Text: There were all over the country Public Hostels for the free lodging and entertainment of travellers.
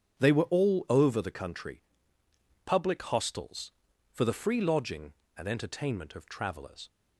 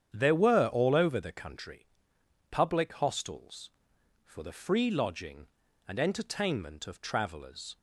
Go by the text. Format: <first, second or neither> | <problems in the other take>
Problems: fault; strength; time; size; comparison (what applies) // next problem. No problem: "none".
second | starts louder than the rest; strong; until 1.2 s; 8 dB; strong in the second // says "They" for "There"; at 0.1 s // pauses between "country" and "Public"; noticeable; at 1.8 s; 0.84 s long; noticeable in the second